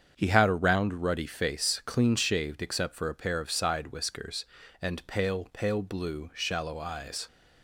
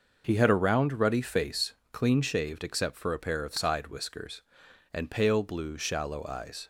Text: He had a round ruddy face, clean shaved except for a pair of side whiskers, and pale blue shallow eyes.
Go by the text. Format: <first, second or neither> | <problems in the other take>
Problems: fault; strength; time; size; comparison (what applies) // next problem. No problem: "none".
second | starts louder than the rest; strong; until 1.2 s; 7.5 dB // says "pale" twice; at 5.5 s